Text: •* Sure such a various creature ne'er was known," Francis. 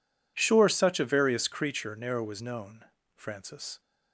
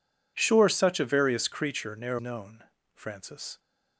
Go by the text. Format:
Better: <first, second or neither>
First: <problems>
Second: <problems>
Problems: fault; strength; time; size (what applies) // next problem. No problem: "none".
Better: first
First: none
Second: skips "was"; at 2.1 s